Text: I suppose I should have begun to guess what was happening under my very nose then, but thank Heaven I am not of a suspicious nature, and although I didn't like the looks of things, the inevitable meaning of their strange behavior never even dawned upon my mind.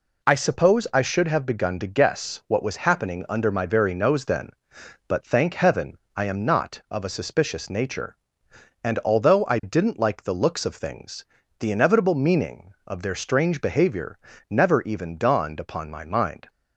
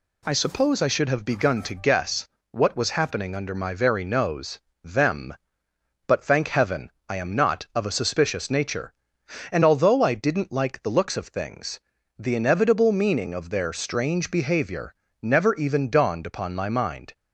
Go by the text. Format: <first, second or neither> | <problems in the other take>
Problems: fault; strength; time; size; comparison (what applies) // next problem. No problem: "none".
first | pauses between "guess" and "what"; slight; at 2.2 s; 0.24 s long // says "them" for "then"; at 4.8 s // pauses between "Heaven" and "I"; slight; at 6.9 s; 0.18 s long; slight in the first // pauses between "behavior" and "never"; slight; at 14.9 s; 0.30 s long; slight in the first